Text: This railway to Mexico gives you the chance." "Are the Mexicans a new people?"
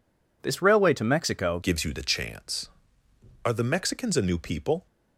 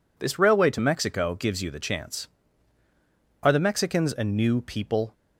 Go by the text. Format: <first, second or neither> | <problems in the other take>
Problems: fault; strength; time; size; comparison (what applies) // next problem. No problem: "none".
second | changes voice at "gives"; from 1.6 s on; 3.2 s long